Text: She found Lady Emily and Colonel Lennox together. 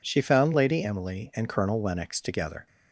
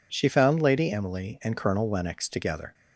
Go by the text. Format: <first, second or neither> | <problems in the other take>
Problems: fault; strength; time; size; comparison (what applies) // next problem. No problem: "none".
neither | none